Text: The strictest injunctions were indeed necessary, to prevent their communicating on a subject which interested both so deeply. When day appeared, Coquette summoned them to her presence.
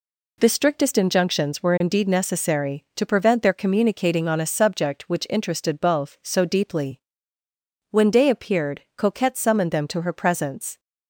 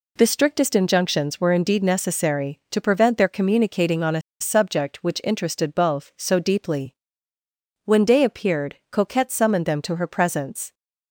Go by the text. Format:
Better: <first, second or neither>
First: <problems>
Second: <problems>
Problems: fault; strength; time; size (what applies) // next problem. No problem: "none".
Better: first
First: none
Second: pauses between "a" and "subject"; slight; at 4.2 s; 0.21 s long